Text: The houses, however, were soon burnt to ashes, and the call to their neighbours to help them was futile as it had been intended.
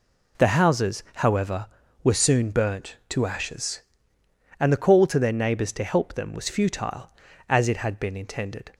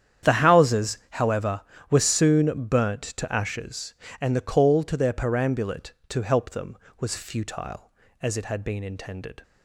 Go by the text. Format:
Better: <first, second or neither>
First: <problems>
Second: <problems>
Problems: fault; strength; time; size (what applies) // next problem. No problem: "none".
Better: first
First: none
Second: starts louder than the rest; strong; until 1.3 s; 9 dB // says "perambulate" for "neighbours"; at 5.1 s